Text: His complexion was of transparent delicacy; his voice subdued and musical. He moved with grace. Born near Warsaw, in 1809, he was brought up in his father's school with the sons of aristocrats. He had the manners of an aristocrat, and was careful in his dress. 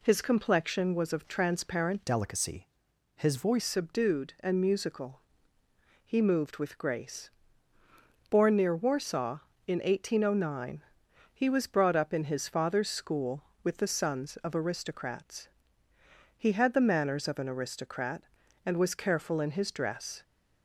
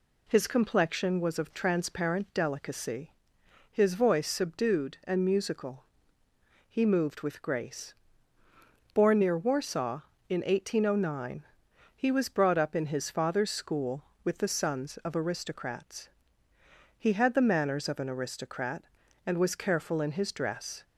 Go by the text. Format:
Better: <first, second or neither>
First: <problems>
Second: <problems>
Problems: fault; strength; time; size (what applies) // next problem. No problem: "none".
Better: second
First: changes voice from "delicacy" to "voice"; from 2.0 to 3.6 s; 1.6 s long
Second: none